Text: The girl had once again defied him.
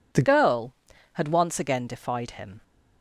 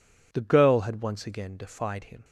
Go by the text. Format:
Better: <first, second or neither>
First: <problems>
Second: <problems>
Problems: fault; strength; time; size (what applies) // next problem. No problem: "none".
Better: second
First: changes voice at "girl"; from 0.2 s on; 2.4 s long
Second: none